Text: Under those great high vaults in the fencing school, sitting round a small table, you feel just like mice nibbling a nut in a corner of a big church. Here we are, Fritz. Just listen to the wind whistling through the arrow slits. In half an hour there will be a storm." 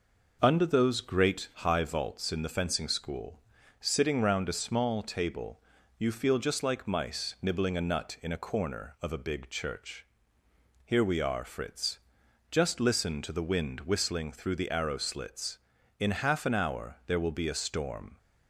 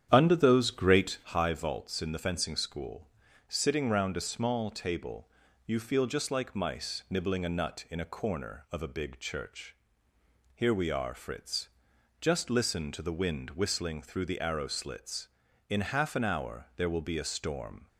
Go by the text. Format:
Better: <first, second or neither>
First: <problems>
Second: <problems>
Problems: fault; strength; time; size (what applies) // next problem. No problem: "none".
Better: first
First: none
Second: starts louder than the rest; strong; until 1.4 s; 9.5 dB